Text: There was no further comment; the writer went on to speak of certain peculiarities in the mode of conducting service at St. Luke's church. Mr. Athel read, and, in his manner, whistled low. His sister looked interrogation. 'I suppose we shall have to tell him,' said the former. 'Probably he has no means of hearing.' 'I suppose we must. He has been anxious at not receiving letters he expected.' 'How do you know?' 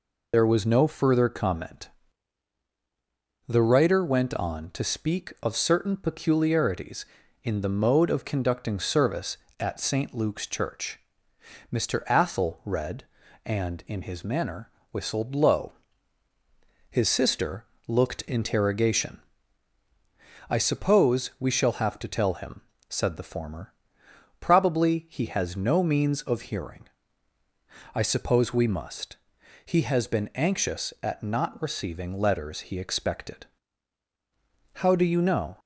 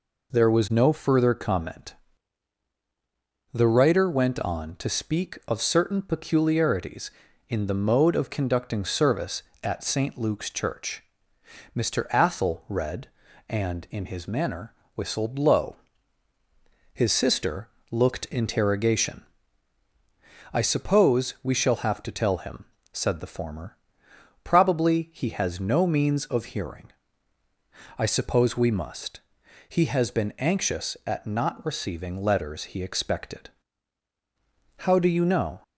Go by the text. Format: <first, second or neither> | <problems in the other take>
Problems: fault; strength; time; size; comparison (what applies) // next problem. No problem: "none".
second | loses the start of "There"; at 0.3 s; 65 ms // pauses between "sister" and "looked"; slight; at 17.6 s; 0.22 s long; slight in the second